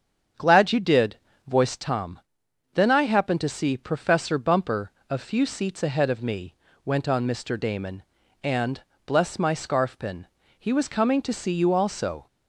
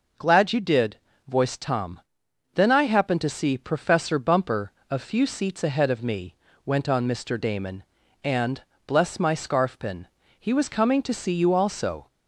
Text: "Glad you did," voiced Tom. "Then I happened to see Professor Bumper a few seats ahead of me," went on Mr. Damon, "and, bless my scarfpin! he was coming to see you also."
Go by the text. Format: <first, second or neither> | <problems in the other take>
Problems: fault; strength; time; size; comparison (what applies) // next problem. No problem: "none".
second | starts louder than the rest; strong; until 2.0 s; 7.5 dB // pauses between "Bumper" and "a"; slight; at 4.9 s; 0.18 s long; slight in the second